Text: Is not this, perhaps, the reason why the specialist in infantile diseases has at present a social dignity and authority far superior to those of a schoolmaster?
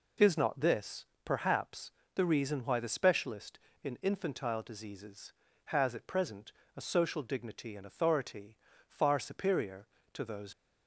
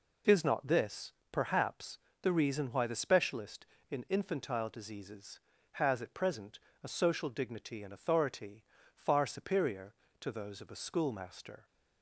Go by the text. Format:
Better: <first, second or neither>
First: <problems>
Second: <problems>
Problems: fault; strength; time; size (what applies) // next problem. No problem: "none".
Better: second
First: pauses between "present" and "a"; slight; at 6.5 s; 0.24 s long // pauses between "authority" and "far"; slight; at 8.5 s; 0.32 s long // stops before "of a schoolmaster"; at 10.5 s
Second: pauses between "present" and "a"; slight; at 6.5 s; 0.24 s long // pauses between "authority" and "far"; slight; at 8.6 s; 0.32 s long